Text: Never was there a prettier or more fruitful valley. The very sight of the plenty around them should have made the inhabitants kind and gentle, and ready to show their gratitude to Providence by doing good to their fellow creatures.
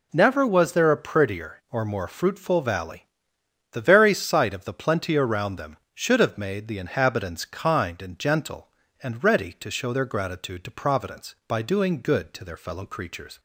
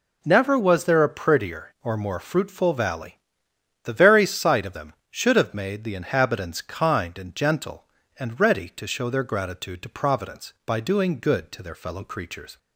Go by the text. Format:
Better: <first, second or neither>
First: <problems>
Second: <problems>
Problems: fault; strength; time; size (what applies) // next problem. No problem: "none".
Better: first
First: none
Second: skips "the plenty around"; at 4.7 s